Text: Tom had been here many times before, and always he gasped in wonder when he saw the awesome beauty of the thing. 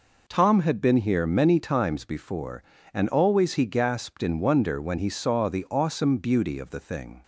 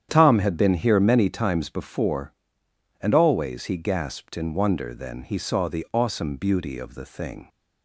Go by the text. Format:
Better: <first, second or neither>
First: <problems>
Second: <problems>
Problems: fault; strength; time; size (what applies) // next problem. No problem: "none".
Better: first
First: none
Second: starts louder than the rest; strong; until 1.1 s; 9 dB // says "then" for "when"; at 4.9 s